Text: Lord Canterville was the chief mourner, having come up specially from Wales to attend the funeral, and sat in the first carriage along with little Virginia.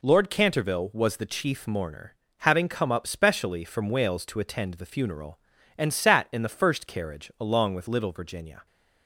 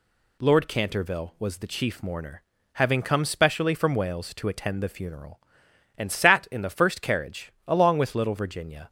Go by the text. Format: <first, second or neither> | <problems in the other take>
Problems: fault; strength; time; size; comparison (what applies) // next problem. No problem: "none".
first | skips "up"; at 3.2 s // pauses between "carriage" and "along"; slight; at 7.5 s; 0.16 s long